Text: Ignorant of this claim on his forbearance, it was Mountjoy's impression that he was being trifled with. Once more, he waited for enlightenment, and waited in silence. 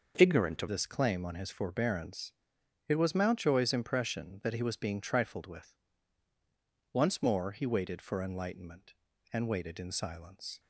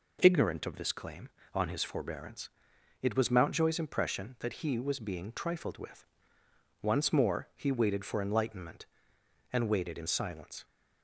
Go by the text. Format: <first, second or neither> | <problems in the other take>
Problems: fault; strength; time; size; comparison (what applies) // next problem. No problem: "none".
second | starts louder than the rest; noticeable; until 1.1 s; 6 dB // changes voice at "this"; from 0.6 s on; 9.9 s long